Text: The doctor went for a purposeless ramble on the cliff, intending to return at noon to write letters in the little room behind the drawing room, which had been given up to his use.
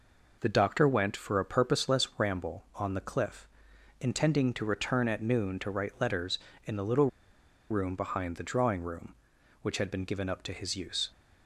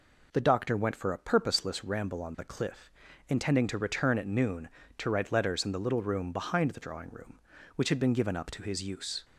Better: second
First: pauses between "little" and "room"; noticeable; at 7.0 s; 0.62 s long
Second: none

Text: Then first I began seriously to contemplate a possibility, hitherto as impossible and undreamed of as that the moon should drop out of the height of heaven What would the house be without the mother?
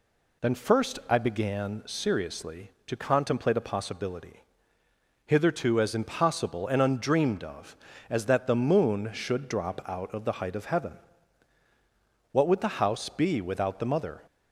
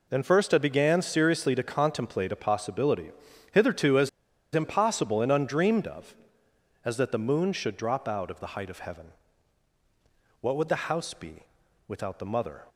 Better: first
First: pauses between "heaven" and "What"; strong; at 10.9 s; 1.3 s long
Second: pauses between "as" and "impossible"; at 4.0 s; 0.44 s long // pauses between "heaven" and "What"; strong; at 9.1 s; 1.2 s long // pauses between "be" and "without"; at 11.4 s; 0.44 s long

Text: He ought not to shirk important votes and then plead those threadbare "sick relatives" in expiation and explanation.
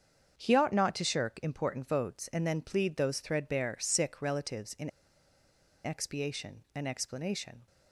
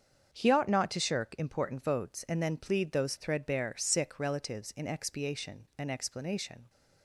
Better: second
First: starts louder than the rest; strong; until 1.4 s; 7.5 dB // pauses between "in" and "expiation"; noticeable; at 4.8 s; 0.94 s long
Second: starts louder than the rest; strong; until 1.3 s; 7 dB

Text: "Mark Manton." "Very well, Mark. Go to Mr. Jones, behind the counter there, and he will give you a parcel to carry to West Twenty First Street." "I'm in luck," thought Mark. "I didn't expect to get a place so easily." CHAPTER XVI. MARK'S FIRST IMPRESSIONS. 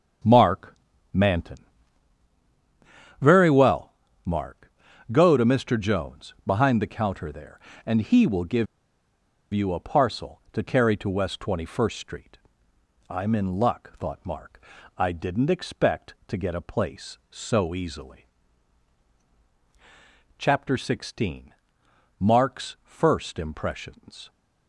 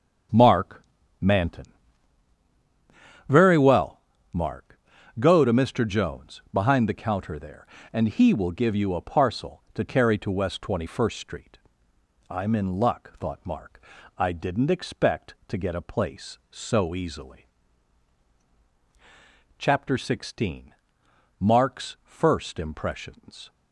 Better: second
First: starts louder than the rest; until 1.6 s; 6.5 dB // pauses between "Mark" and "Manton"; slight; at 0.7 s; 0.36 s long // pauses between "give" and "you"; noticeable; at 8.6 s; 0.87 s long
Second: starts louder than the rest; until 1.6 s; 6.5 dB // pauses between "Mark" and "Manton"; slight; at 0.8 s; 0.36 s long

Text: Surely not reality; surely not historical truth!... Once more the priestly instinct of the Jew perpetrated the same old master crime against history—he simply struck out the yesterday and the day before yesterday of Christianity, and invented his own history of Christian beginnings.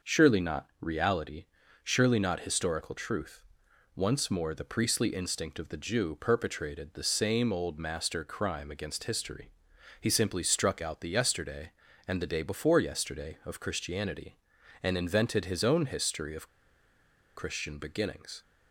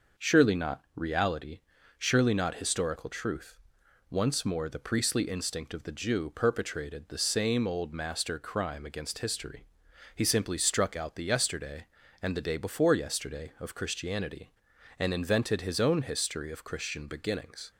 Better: second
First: pauses between "of" and "Christian"; noticeable; at 16.4 s; 0.88 s long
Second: none

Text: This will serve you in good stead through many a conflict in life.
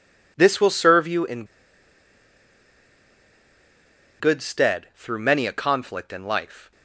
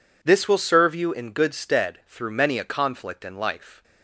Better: second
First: pauses between "in" and "good"; strong; at 1.4 s; 2.7 s long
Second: none

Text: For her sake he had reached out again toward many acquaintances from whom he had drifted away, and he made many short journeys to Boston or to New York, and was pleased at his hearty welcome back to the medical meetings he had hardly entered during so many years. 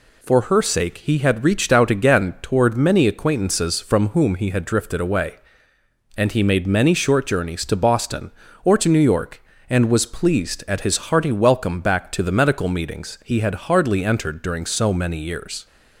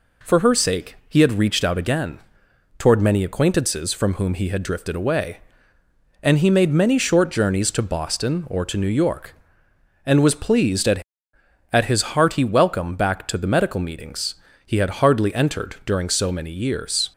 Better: first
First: none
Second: pauses between "again" and "toward"; noticeable; at 2.1 s; 0.60 s long // says "at" twice; at 11.7 s // pauses between "meetings" and "he"; slight; at 14.3 s; 0.32 s long

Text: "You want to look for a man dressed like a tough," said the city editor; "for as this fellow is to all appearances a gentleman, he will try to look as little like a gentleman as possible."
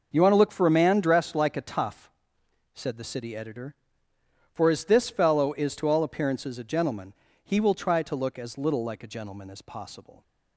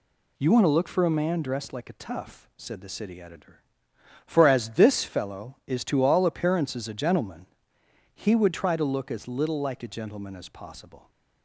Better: first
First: none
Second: says "would" for "will"; at 8.3 s

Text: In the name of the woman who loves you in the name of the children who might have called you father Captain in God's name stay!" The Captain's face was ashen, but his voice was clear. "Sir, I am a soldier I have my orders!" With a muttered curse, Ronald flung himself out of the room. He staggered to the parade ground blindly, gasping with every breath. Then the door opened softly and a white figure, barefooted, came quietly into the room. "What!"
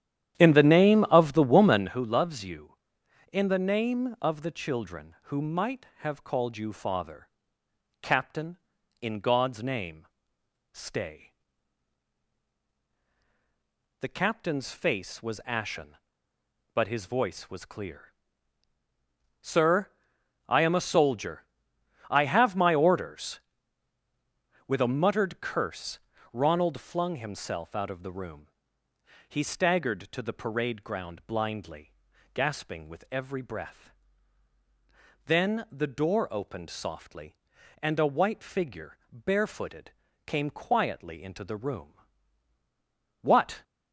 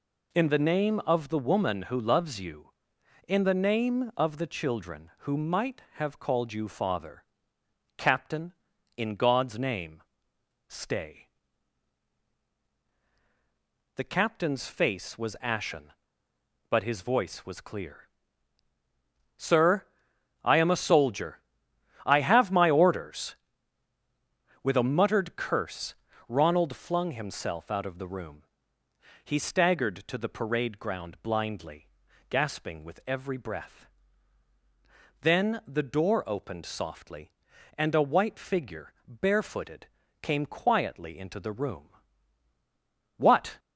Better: second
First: starts louder than the rest; strong; until 2.0 s; 10.5 dB // pauses between "father" and "Captain"; noticeable; at 7.2 s; 0.72 s long // pauses between "name" and "stay"; noticeable; at 10.0 s; 0.66 s long // pauses between "soldier" and "I"; noticeable; at 21.4 s; 0.66 s long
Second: pauses between "father" and "Captain"; noticeable; at 7.2 s; 0.72 s long // pauses between "name" and "stay"; noticeable; at 10.0 s; 0.66 s long // pauses between "soldier" and "I"; noticeable; at 21.4 s; 0.66 s long

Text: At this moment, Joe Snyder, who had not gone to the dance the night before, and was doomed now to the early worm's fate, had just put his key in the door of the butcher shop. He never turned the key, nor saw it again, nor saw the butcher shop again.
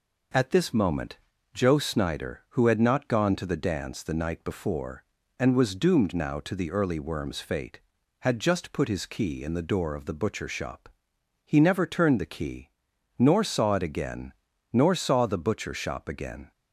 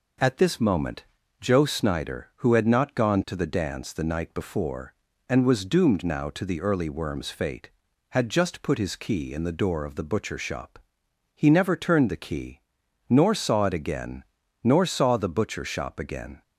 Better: neither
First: none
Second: none

